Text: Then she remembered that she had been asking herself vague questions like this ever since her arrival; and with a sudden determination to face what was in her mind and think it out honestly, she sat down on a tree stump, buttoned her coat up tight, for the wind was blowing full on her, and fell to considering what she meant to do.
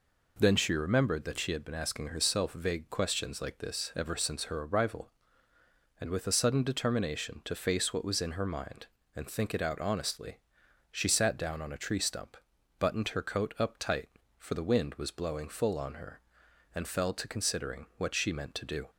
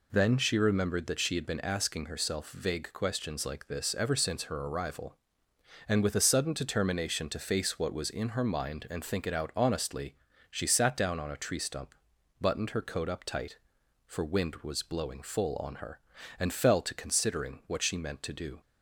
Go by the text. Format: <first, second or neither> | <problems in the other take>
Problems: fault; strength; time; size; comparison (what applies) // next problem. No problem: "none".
first | skips "the"; at 14.2 s